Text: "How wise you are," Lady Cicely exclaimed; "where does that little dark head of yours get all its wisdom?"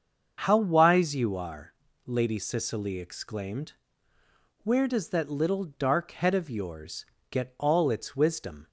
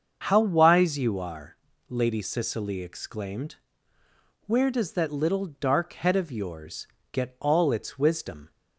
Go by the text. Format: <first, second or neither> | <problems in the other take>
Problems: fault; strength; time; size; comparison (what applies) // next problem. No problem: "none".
neither | starts louder than the rest; the same in both // pauses between "yours" and "get"; slight; the same in both